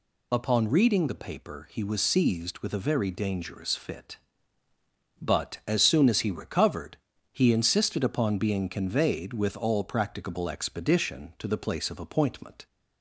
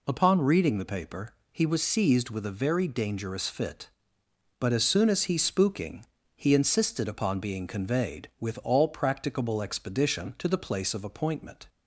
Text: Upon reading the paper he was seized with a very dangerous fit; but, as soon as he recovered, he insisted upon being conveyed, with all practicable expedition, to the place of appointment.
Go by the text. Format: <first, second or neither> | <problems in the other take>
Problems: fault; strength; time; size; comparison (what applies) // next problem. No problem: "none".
first | pauses between "paper" and "he"; slight; at 1.3 s; 0.18 s long // says "spooking" for "recovered"; at 5.3 s